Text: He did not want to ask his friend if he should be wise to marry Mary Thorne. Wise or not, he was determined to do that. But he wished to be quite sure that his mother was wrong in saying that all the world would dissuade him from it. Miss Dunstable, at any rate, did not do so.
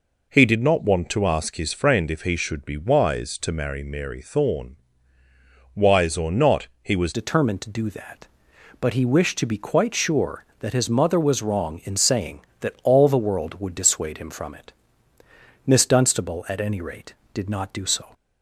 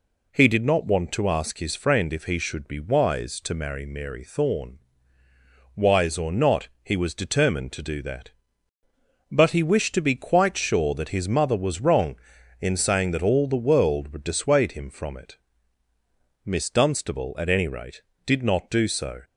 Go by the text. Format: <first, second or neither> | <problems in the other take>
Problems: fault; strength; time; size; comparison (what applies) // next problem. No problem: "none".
second | changes voice at "determined"; from 7.1 s on; 11.0 s long